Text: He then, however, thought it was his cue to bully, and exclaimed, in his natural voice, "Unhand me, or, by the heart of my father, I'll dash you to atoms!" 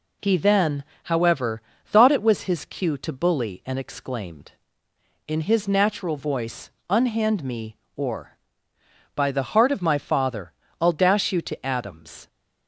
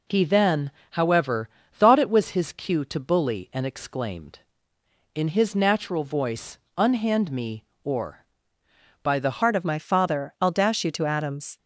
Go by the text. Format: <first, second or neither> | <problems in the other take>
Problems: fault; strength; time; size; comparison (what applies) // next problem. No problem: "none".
first | changes voice at "heart"; from 9.4 s on; 2.1 s long